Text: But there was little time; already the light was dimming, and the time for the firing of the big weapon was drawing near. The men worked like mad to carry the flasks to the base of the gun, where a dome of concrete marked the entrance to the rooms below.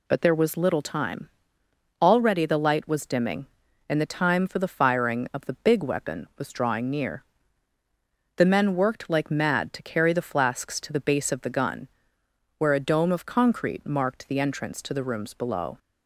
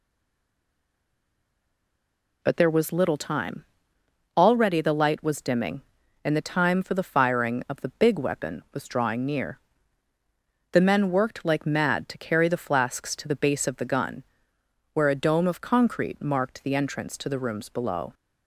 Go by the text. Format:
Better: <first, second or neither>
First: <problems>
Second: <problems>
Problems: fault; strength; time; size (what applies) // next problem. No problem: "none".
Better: first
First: none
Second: stays silent before the first word; until 2.4 s; 2.4 s long